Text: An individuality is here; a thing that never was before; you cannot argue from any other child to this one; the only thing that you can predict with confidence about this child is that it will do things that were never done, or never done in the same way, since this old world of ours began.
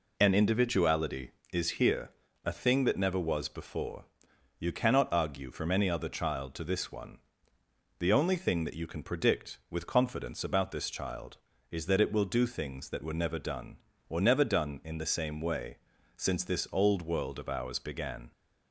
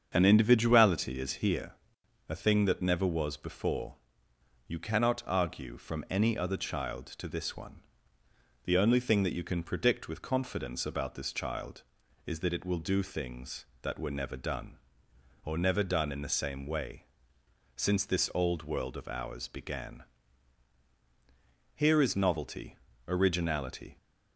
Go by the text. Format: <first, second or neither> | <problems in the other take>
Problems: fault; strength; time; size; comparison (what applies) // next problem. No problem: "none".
first | starts louder than the rest; strong; until 1.1 s; 7 dB // goes on to say "Here is novelty originality"; strong; from 21.7 s on; 2.2 s long